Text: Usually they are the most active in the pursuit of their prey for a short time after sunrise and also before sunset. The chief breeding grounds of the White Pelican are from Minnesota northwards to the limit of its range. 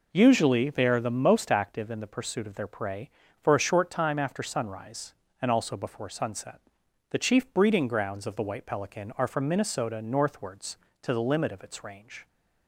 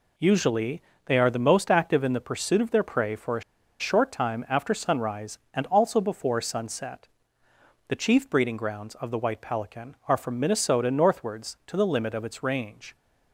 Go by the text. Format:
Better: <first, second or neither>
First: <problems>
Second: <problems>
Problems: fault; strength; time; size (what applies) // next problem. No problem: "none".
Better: first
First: none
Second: pauses between "Usually" and "they"; slight; at 0.8 s; 0.26 s long // pauses between "a" and "short"; at 3.4 s; 0.39 s long